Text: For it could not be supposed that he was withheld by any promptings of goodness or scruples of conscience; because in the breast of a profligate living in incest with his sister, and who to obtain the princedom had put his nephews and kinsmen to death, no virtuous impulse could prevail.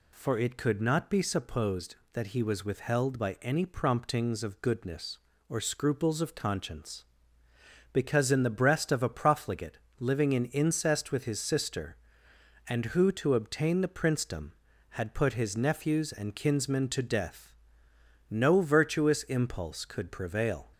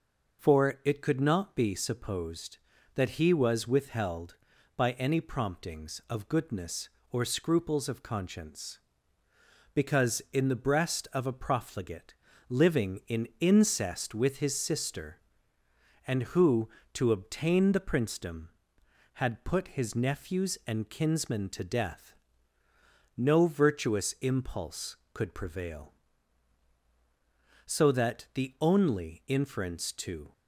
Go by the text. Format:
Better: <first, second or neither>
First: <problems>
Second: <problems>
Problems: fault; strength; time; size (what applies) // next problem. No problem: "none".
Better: first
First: pauses between "profligate" and "living"; slight; at 9.7 s; 0.20 s long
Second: pauses between "profligate" and "living"; slight; at 12.1 s; 0.34 s long // goes on to say "So that the only inference to"; strong; from 27.6 s on; 2.6 s long